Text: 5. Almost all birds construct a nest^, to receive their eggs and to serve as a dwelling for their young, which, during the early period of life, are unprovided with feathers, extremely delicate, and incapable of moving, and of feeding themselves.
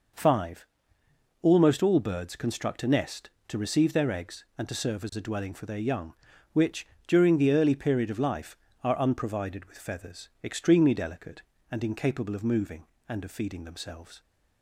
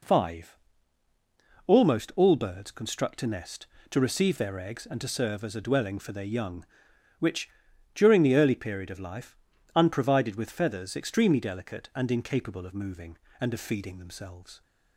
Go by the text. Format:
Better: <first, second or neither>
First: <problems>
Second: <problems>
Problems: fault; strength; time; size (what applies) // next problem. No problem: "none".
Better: first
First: none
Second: skips "are"; at 9.5 s